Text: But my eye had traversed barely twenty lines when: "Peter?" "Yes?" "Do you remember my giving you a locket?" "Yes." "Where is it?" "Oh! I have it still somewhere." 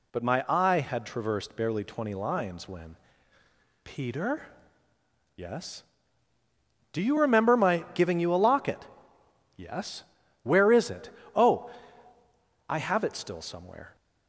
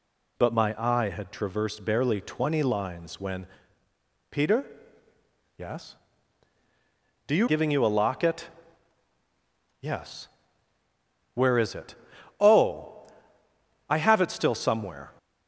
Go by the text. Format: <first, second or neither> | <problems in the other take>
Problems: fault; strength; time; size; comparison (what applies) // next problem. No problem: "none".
first | skips "remember my"; at 7.4 s